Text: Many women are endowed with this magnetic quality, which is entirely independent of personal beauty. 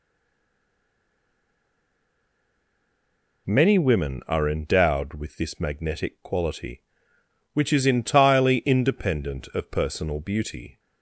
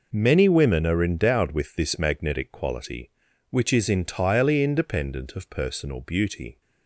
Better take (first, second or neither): second